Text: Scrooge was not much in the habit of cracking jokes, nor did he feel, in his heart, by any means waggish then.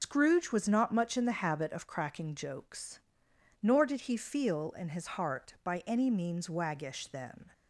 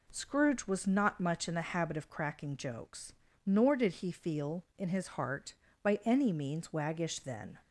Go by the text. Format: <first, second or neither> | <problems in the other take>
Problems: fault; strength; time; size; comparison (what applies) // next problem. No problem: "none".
second | loses the start of "Scrooge"; at 0.0 s; 105 ms // pauses between "his" and "heart"; slight; at 5.0 s; 0.16 s long